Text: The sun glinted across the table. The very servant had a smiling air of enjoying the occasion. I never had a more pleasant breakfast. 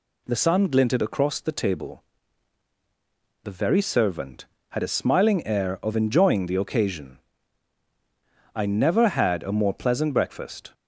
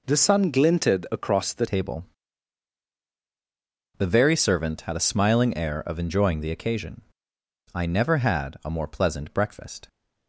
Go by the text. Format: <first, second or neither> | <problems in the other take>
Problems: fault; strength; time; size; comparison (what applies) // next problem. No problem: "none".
first | changes voice at "table"; from 1.6 s on; 8.2 s long